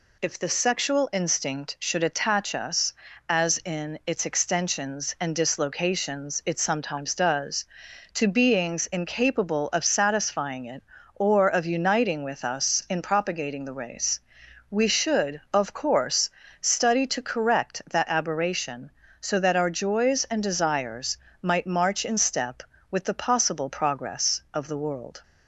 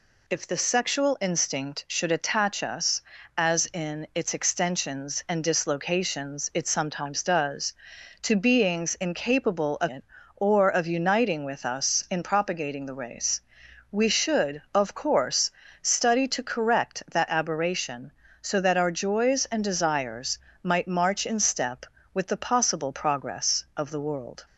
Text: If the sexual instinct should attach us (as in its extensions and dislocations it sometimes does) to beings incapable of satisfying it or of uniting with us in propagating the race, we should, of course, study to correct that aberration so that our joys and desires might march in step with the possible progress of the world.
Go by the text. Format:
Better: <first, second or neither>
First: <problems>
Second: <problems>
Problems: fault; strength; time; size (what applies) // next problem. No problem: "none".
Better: first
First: pauses between "desires" and "might"; slight; at 21.1 s; 0.26 s long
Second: skips "satisfying"; at 9.8 s // pauses between "desires" and "might"; slight; at 20.3 s; 0.26 s long